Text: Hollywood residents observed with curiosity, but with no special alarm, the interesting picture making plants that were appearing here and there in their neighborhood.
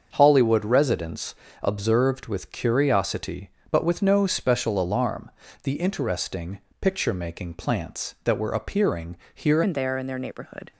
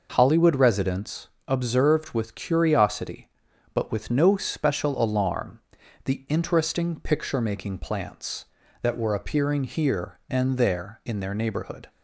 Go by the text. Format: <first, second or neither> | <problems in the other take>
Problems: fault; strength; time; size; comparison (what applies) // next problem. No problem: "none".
second | starts louder than the rest; until 1.1 s; 6.5 dB // pauses between "residents" and "observed"; slight; at 1.3 s; 0.28 s long; slight in the second // pauses between "interesting" and "picture"; slight; at 6.5 s; 0.22 s long // pauses between "appearing" and "here"; slight; at 9.1 s; 0.18 s long // changes voice at "and"; from 9.6 s on; 1.1 s long